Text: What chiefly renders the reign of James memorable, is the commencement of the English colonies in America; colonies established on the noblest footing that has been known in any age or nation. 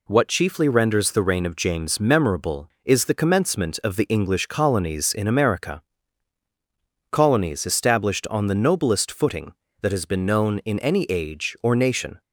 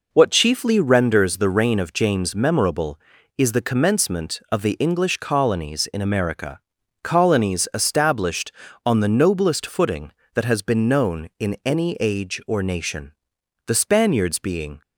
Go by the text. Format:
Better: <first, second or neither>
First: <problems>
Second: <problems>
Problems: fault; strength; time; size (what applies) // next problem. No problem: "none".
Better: first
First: none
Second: goes on to say "The Spaniards being"; noticeable; from 13.6 s on; 1.1 s long